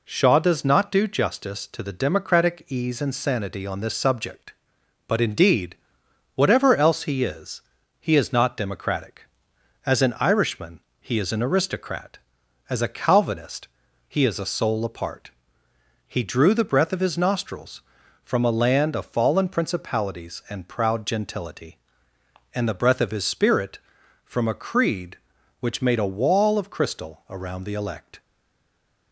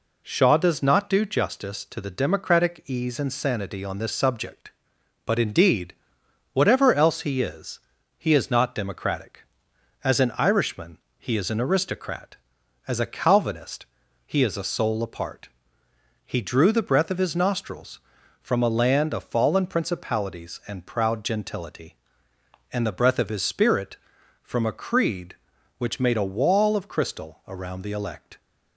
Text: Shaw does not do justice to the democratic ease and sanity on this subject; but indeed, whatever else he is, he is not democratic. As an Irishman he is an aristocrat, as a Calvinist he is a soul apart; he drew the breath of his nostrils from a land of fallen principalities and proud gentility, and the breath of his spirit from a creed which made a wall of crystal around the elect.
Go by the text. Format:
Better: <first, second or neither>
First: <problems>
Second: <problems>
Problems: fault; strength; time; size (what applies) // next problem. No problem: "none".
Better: second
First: pauses between "Irishman" and "he"; slight; at 10.7 s; 0.22 s long // pauses between "Calvinist" and "he"; at 13.6 s; 0.40 s long // stays silent after the last word; slight; from 28.2 s on; 0.9 s long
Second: pauses between "Irishman" and "he"; slight; at 10.9 s; 0.22 s long // pauses between "Calvinist" and "he"; at 13.8 s; 0.40 s long